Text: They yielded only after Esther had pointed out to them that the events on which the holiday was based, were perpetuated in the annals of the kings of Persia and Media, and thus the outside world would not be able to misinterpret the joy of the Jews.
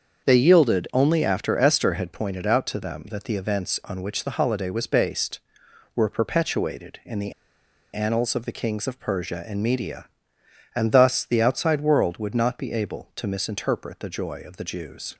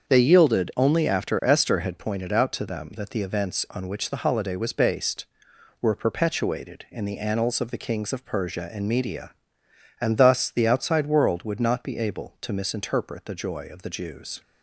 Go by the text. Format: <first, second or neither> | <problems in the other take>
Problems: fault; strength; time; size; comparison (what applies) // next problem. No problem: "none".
second | starts louder than the rest; until 1.3 s; 7 dB; also in the second // pauses between "the" and "annals"; noticeable; at 7.3 s; 0.60 s long